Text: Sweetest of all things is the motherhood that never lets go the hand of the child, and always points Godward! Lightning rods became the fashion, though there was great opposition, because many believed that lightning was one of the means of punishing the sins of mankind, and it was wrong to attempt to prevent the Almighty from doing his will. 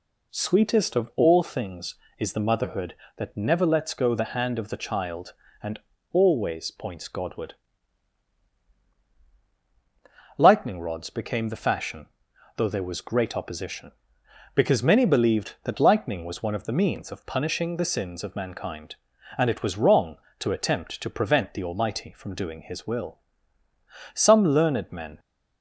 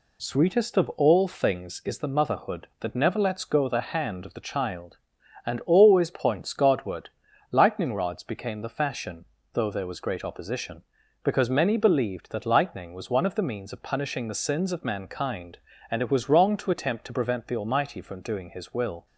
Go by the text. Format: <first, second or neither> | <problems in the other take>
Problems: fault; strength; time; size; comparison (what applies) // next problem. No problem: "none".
second | pauses between "and" and "always"; slight; at 5.8 s; 0.32 s long // goes on to say "Some learned men"; noticeable; from 24.1 s on; 1.0 s long